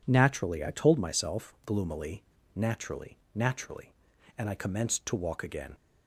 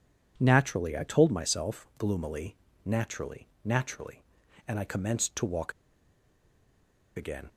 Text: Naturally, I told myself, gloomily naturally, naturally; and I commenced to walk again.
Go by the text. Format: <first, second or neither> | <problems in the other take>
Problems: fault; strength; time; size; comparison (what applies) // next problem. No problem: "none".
first | pauses between "gloomily" and "naturally"; slight; at 2.5 s; 0.28 s long; slight in the first // pauses between "walk" and "again"; strong; at 5.7 s; 1.4 s long